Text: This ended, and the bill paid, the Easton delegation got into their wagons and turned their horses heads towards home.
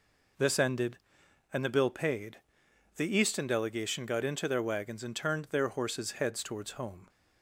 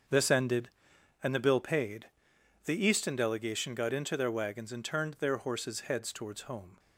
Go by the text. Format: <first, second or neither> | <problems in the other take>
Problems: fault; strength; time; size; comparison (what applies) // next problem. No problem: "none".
first | gets quieter; strong; throughout; 11.5 dB